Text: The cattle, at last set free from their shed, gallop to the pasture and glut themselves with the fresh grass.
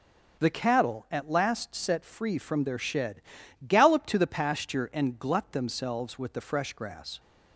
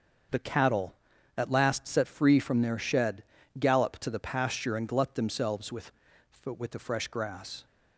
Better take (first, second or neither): first